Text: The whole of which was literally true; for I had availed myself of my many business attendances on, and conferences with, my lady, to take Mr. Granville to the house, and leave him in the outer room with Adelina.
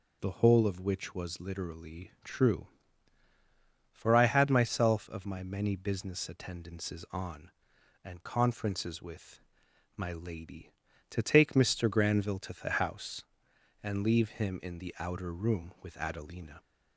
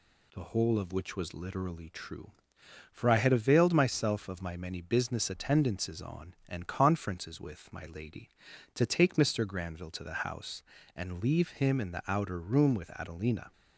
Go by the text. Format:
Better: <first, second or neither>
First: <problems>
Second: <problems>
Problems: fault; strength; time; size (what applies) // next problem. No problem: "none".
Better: second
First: skips "availed"; at 4.4 s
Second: none